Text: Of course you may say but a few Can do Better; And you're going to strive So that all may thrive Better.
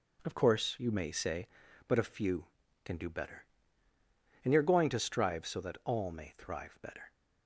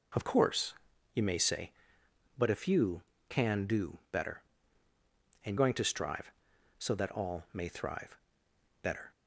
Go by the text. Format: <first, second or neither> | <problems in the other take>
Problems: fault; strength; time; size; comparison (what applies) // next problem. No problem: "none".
first | pauses between "course" and "you"; at 0.7 s; 0.42 s long // skips "you're"; at 5.5 s // pauses between "thrive" and "Better"; noticeable; at 8.1 s; 0.66 s long